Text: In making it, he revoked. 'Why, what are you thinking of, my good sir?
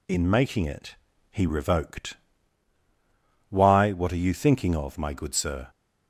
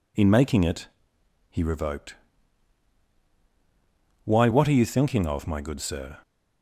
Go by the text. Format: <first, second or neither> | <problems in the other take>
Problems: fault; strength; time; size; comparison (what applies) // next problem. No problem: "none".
neither | none